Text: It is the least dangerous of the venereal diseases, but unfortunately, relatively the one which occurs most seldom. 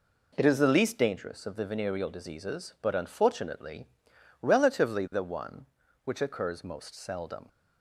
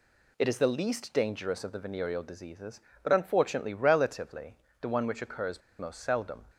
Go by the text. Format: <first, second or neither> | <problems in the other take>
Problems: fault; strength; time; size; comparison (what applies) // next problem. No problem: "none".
first | pauses between "relatively" and "the"; slight; at 4.5 s; 0.24 s long // pauses between "occurs" and "most"; slight; at 5.6 s; 0.18 s long